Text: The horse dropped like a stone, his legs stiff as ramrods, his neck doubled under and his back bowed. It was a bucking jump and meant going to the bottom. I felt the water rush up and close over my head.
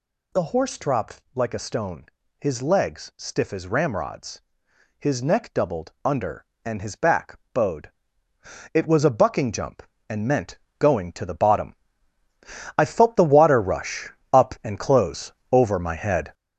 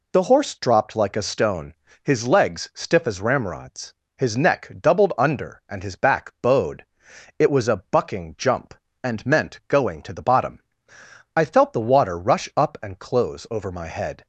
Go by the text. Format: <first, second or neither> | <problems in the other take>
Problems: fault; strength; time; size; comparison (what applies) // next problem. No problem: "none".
second | gets louder; throughout; 6.5 dB // pauses between "back" and "bowed"; slight; at 7.3 s; 0.16 s long // pauses between "meant" and "going"; slight; at 10.5 s; 0.22 s long // pauses between "rush" and "up"; slight; at 14.0 s; 0.24 s long // pauses between "close" and "over"; slight; at 15.3 s; 0.20 s long